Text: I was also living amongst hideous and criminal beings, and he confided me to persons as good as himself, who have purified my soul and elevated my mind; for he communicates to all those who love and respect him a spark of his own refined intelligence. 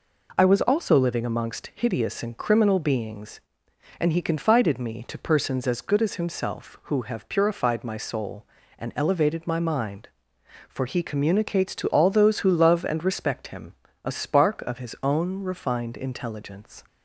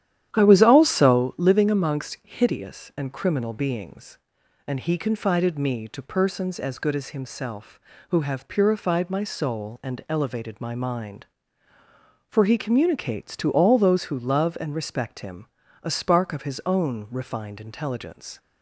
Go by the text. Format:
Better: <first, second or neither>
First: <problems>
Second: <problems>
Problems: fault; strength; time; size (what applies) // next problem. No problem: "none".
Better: first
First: pauses between "him" and "a"; slight; at 13.7 s; 0.30 s long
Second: starts louder than the rest; strong; until 1.4 s; 11 dB // pauses between "him" and "a"; slight; at 15.4 s; 0.36 s long